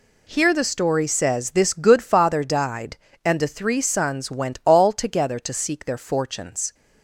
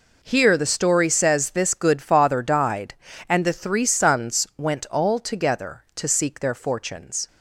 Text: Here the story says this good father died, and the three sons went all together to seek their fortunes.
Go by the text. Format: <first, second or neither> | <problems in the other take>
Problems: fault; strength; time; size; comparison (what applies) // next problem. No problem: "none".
neither | none